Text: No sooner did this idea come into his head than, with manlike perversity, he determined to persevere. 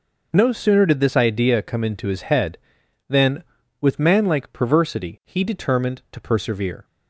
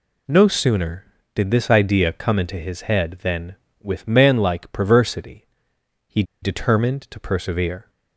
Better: first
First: none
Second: pauses between "he" and "determined"; slight; at 6.2 s; 0.19 s long

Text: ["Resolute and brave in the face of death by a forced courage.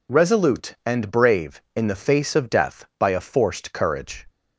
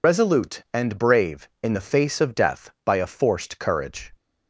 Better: first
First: none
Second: loses the start of "Resolute"; at 0.0 s; 65 ms

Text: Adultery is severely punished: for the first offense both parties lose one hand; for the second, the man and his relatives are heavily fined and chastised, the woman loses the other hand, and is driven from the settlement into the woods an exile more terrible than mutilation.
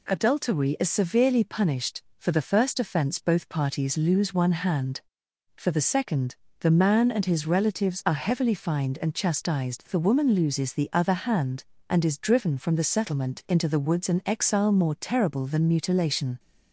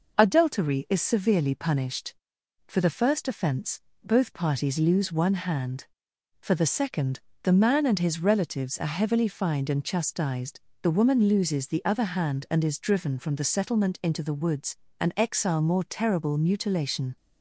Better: first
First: none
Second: pauses between "offense" and "both"; slight; at 3.8 s; 0.22 s long // pauses between "woods" and "an"; slight; at 14.7 s; 0.24 s long // skips "than"; at 16.3 s

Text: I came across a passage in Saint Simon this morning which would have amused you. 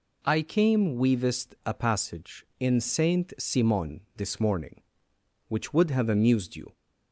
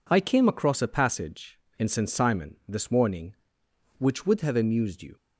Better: second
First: says "weavest" for "across"; at 0.9 s // pauses between "Simon" and "this"; slight; at 4.0 s; 0.16 s long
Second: none

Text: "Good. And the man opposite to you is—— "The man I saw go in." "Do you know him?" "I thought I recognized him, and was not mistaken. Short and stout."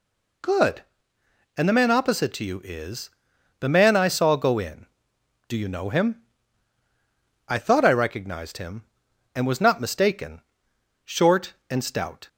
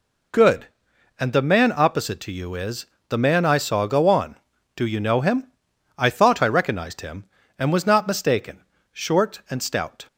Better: first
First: none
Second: says "on" for "in"; at 4.0 s

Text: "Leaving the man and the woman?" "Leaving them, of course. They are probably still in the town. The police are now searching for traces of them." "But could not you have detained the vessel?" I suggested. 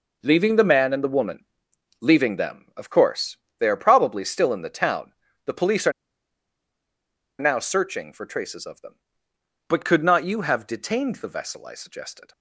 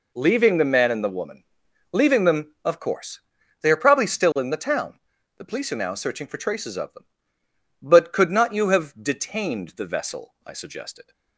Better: second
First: pauses between "are" and "now"; strong; at 5.9 s; 1.4 s long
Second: none

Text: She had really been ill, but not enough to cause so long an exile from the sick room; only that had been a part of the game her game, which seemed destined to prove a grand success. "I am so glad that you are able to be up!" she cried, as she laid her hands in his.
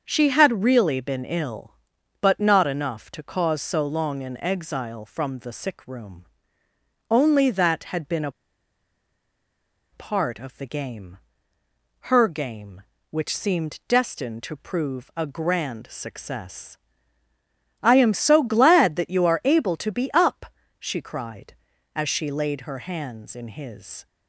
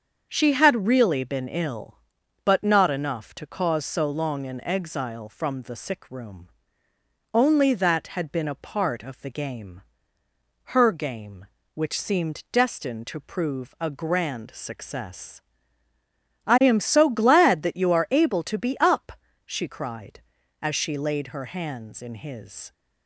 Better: second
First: starts louder than the rest; until 1.0 s; 7 dB // pauses between "a" and "part"; strong; at 8.2 s; 1.6 s long // pauses between "game" and "her"; noticeable; at 11.1 s; 0.94 s long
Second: starts louder than the rest; until 1.3 s; 7 dB // pauses between "game" and "her"; noticeable; at 9.8 s; 0.94 s long

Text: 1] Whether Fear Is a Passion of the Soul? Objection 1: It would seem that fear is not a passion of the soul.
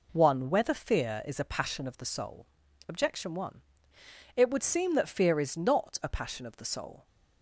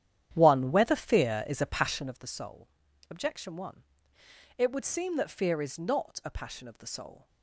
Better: first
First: none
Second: starts louder than the rest; strong; until 2.2 s; 10.5 dB

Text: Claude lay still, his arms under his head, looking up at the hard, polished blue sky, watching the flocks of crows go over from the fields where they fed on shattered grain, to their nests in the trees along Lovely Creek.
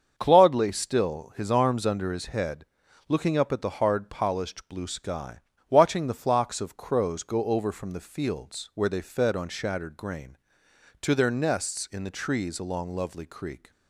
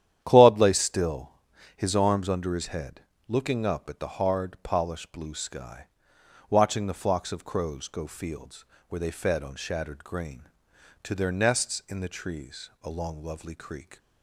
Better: first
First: starts louder than the rest; until 1.1 s; 7 dB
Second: starts louder than the rest; strong; until 1.2 s; 10.5 dB // skips "over from the"; at 8.0 s // pauses between "fields" and "where"; slight; at 8.6 s; 0.24 s long

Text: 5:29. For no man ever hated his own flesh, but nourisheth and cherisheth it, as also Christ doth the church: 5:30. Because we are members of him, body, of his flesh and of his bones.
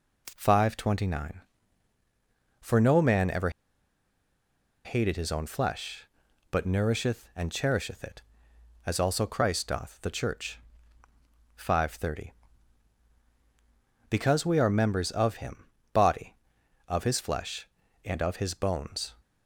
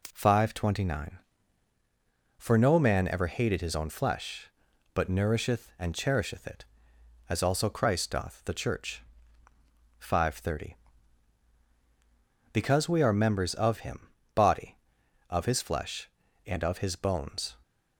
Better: second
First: pauses between "ever" and "hated"; strong; at 3.4 s; 1.3 s long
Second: none

